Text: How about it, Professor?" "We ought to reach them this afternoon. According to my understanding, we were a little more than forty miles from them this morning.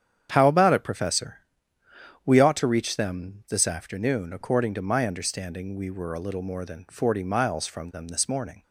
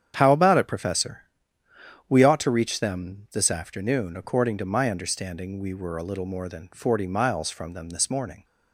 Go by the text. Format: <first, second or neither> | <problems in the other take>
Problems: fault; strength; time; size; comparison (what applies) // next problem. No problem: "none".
neither | starts louder than the rest; strong; the same in both